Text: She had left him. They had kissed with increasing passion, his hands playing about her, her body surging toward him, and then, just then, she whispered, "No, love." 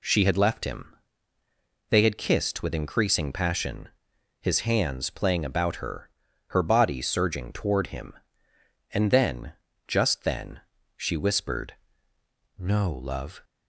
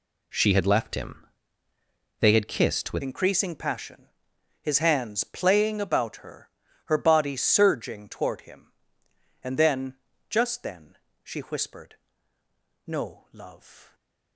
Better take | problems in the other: first | changes voice at "increasing"; from 3.0 s on; 10.9 s long

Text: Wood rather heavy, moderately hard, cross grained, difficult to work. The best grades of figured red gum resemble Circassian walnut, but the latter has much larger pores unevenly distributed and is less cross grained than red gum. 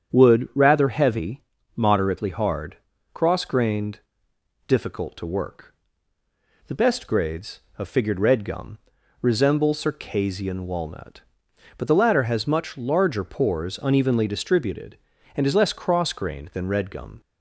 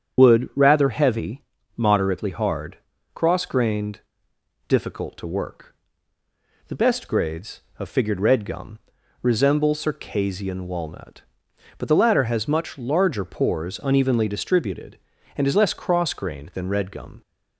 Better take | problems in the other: first | loses the start of "Wood"; at 0.1 s; 55 ms // starts louder than the rest; strong; until 1.2 s; 8 dB; strong in the first // pauses between "gum" and "resemble"; at 8.7 s; 0.44 s long; also in the first

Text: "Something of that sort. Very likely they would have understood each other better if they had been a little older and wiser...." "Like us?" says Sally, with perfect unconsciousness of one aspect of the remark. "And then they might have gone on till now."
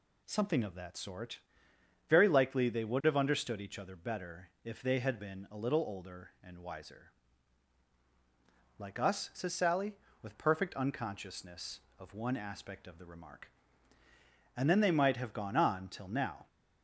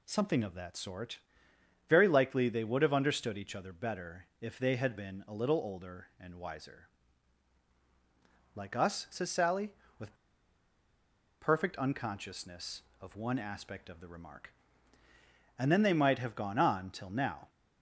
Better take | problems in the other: first | pauses between "with" and "perfect"; strong; at 10.1 s; 1.2 s long

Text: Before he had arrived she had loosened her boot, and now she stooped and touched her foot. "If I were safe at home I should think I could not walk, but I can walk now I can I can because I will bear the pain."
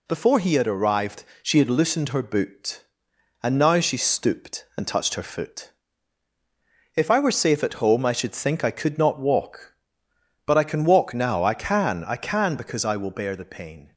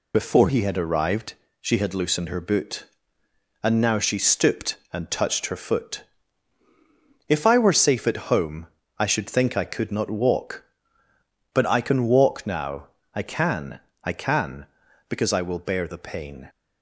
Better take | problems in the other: first | loses the start of "Before"; at 0.1 s; 50 ms // pauses between "arrived" and "she"; slight; at 1.3 s; 0.28 s long; slight in the first // pauses between "home" and "I"; slight; at 8.6 s; 0.32 s long // pauses between "now" and "I"; slight; at 12.8 s; 0.26 s long // pauses between "can" and "I"; slight; at 13.8 s; 0.22 s long

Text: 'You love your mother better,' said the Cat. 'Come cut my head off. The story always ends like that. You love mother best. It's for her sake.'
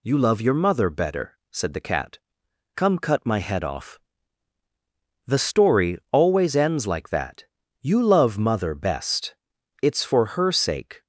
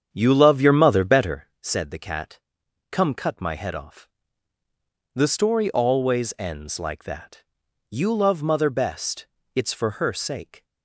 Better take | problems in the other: first | starts louder than the rest; strong; until 1.5 s; 8 dB

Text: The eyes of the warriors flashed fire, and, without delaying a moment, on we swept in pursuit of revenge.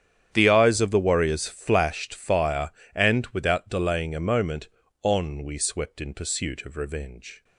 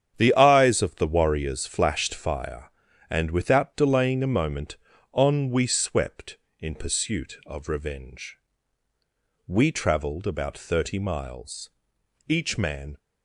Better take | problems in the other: first | starts louder than the rest; strong; until 1.2 s; 9 dB; strong in the first // goes on to say "We travelled about thirty miles each man"; strong; from 9.4 s on; 3.5 s long

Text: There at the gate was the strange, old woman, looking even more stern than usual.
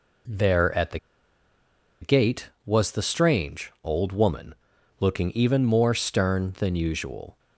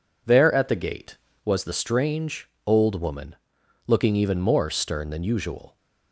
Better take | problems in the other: second | pauses between "the" and "gate"; at 0.9 s; 1.0 s long

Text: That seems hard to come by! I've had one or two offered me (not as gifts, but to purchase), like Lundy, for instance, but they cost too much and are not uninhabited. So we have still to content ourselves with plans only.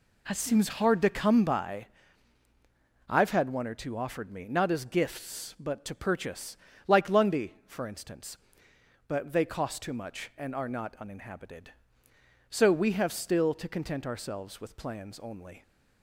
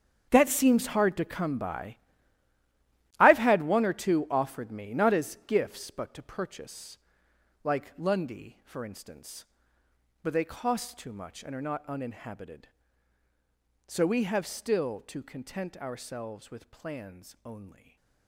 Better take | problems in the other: first | gets quieter; strong; throughout; 14 dB // stays silent after the last word; slight; from 17.6 s on; 0.6 s long

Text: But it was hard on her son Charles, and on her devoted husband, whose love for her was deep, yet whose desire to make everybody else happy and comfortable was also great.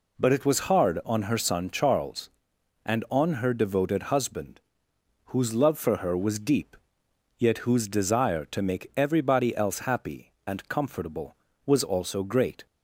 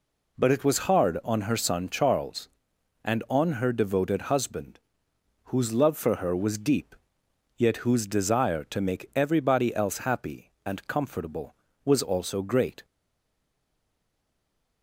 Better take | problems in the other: first | stays silent after the last word; noticeable; from 12.8 s on; 2.0 s long

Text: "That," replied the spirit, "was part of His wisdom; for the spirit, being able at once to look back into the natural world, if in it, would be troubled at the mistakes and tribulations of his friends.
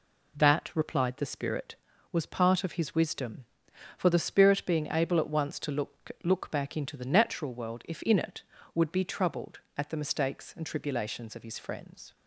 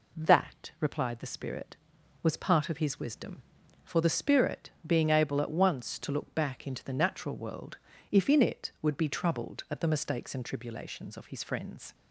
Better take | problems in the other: second | says "look" twice; at 6.2 s

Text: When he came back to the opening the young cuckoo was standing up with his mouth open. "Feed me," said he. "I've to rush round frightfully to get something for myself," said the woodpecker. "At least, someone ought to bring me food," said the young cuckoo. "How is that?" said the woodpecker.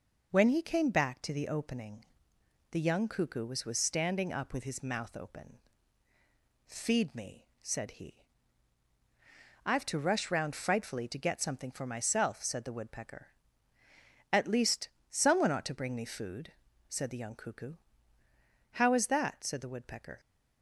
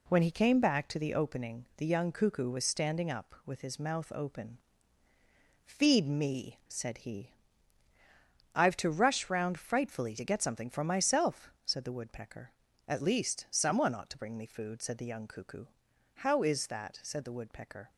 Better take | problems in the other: second | pauses between "opening" and "the"; noticeable; at 2.0 s; 0.66 s long // says "was" twice; at 3.6 s

